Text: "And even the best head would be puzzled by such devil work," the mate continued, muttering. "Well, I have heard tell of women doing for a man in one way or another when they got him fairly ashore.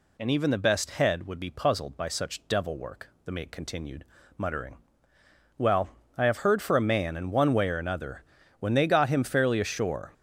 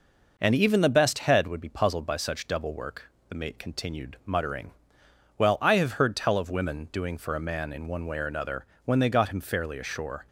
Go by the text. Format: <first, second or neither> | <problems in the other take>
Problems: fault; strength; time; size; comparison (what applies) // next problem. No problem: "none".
second | skips "tell of women doing"; at 6.6 s // pauses between "another" and "when"; slight; at 8.2 s; 0.36 s long; slight in the second